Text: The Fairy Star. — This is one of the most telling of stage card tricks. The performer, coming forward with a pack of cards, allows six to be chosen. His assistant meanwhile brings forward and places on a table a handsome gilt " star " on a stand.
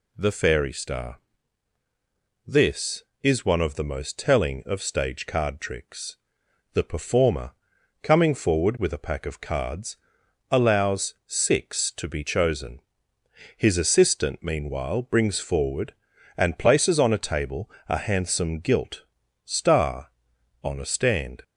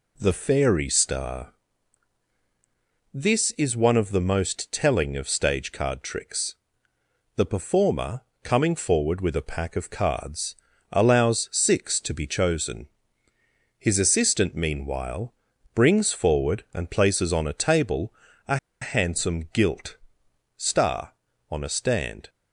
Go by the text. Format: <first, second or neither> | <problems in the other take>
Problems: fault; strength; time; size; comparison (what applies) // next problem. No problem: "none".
first | pauses between "meanwhile" and "brings"; at 15.3 s; 0.40 s long // pauses between "table" and "a"; at 18.1 s; 0.38 s long; slight in the first // pauses between "a" and "handsome"; slight; at 18.5 s; 0.24 s long